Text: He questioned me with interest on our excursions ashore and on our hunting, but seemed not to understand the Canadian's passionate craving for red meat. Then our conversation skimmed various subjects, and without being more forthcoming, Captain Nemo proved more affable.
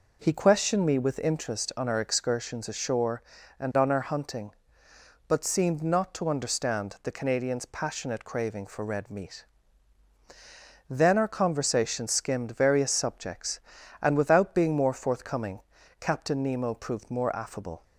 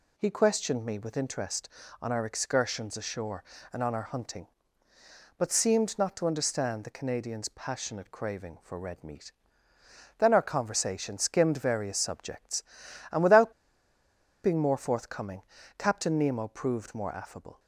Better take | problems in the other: first | pauses between "without" and "being"; noticeable; at 13.5 s; 0.91 s long

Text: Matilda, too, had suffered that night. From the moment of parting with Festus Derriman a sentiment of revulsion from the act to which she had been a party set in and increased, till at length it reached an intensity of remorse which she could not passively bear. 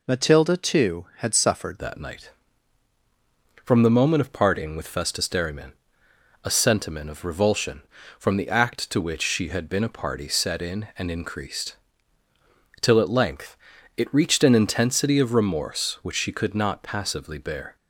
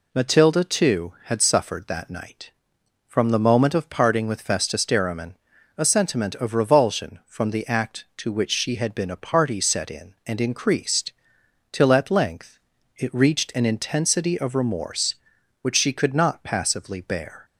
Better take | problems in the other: second | changes voice at "that"; from 1.7 s on; 16.0 s long // pauses between "Derriman" and "a"; noticeable; at 5.7 s; 0.72 s long; also in the second // pauses between "length" and "it"; at 13.5 s; 0.40 s long; also in the second

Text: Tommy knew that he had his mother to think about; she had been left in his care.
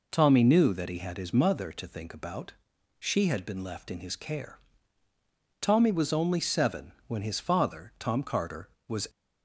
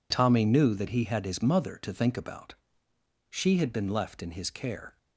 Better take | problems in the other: second | goes on to say "Tommy was only seven when his father Tom Carter was"; strong; from 5.5 s on; 3.4 s long

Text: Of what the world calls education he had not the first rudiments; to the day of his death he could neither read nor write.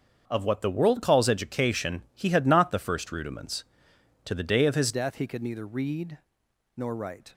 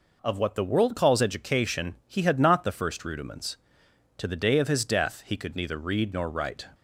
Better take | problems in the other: second | starts louder than the rest; until 1.2 s; 7 dB // changes voice at "death"; from 4.9 s on; 2.4 s long // pauses between "read" and "nor"; noticeable; at 6.1 s; 0.56 s long

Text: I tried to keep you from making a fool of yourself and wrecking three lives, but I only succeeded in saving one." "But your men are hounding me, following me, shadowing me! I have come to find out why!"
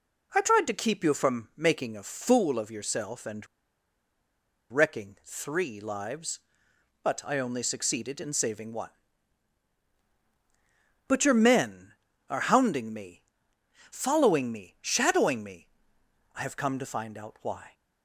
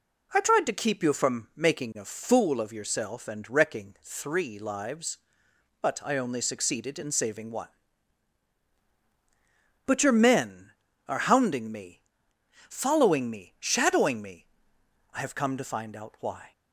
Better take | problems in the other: second | pauses between "and" and "wrecking"; at 3.4 s; 1.2 s long

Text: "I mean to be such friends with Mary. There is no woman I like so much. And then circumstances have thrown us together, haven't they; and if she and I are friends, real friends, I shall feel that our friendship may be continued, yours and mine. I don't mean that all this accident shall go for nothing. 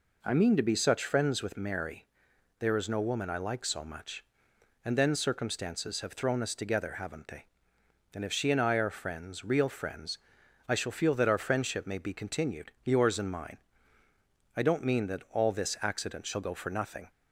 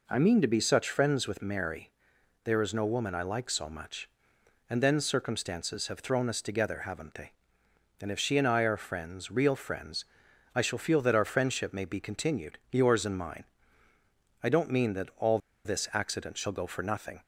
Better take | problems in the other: first | pauses between "all" and "this"; slight; at 15.3 s; 0.25 s long

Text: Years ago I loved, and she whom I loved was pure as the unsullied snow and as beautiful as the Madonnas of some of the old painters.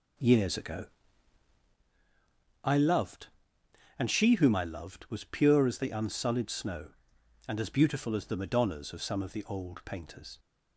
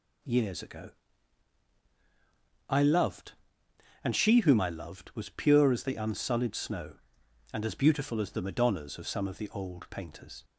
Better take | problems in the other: second | starts louder than the rest; noticeable; until 1.8 s; 5.5 dB // pauses between "ago" and "I"; strong; at 0.8 s; 1.7 s long; strong in the second

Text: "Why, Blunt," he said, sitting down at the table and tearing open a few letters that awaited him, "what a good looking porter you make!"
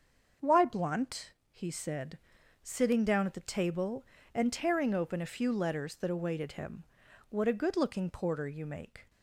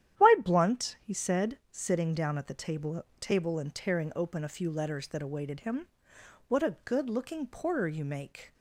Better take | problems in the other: first | starts louder than the rest; strong; until 1.3 s; 11 dB; also in the first // says "table" twice; at 3.1 s

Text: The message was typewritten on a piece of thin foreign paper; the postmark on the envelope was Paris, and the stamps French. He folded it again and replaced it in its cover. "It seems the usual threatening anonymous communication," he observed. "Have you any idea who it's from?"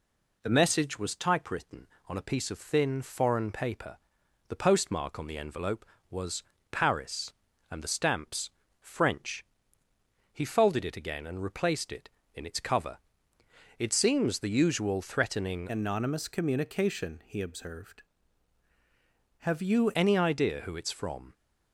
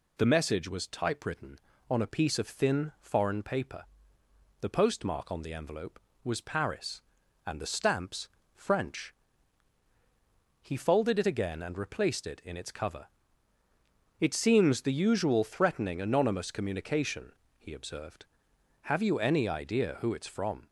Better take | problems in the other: second | pauses between "was" and "Paris"; slight; at 6.4 s; 0.28 s long // pauses between "stamps" and "French"; slight; at 8.4 s; 0.30 s long; slight in the second // changes voice from "anonymous" to "you"; from 15.7 to 19.8 s; 4.1 s long

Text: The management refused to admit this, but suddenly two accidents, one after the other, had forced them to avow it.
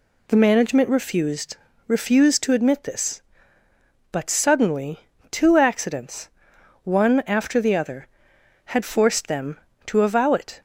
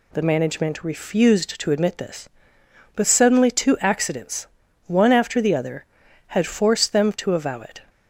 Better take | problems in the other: second | says "refused" twice; at 1.8 s // pauses between "suddenly" and "two"; slight; at 5.0 s; 0.30 s long

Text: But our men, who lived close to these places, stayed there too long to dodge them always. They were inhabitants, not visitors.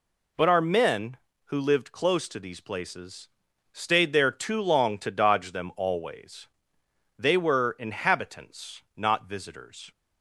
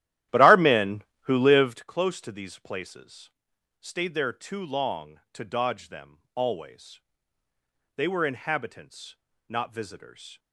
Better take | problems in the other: first | starts louder than the rest; strong; until 1.8 s; 13 dB // pauses between "them" and "always"; slight; at 6.1 s; 0.16 s long

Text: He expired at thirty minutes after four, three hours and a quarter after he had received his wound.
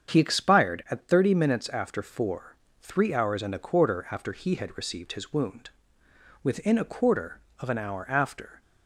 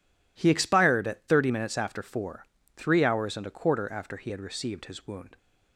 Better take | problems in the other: second | starts louder than the rest; strong; until 1.1 s; 7.5 dB // goes on to say "Within a quarter of an hour after"; strong; from 6.4 s on; 2.1 s long

